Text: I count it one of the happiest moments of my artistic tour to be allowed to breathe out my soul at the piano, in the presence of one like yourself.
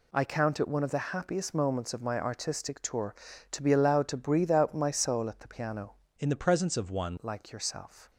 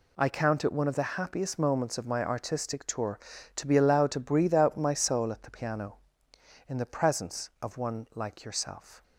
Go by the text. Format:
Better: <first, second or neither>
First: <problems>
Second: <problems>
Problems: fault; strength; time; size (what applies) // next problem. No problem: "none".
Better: second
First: changes voice from "in" to "one"; from 6.1 to 7.1 s; 1.0 s long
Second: none